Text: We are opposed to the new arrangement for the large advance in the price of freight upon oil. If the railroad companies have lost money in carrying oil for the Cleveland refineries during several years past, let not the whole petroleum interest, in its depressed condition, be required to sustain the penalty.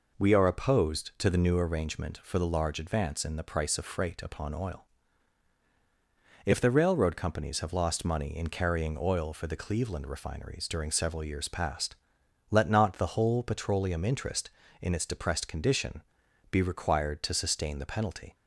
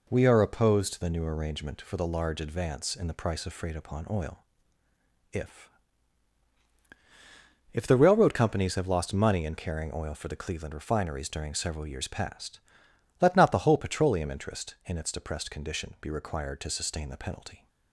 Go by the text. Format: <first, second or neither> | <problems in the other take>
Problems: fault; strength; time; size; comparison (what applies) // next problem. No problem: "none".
first | says "If" twice; at 7.7 s